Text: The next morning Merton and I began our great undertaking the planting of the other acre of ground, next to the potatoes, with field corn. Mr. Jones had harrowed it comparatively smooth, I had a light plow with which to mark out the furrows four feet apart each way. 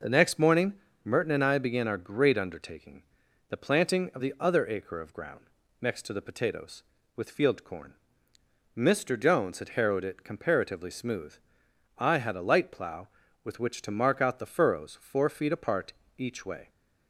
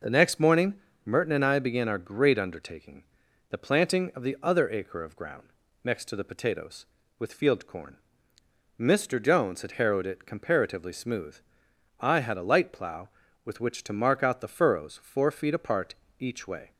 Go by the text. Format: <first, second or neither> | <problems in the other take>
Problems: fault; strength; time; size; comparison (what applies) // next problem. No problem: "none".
neither | pauses between "morning" and "Merton"; slight; the same in both // pauses between "undertaking" and "the"; noticeable; the same in both // pauses between "apart" and "each"; slight; the same in both